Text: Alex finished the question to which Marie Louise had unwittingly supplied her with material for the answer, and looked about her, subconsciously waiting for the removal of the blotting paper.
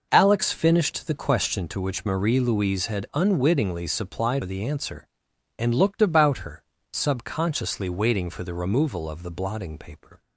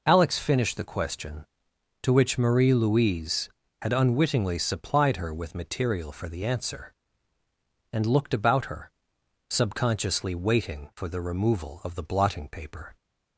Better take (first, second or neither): second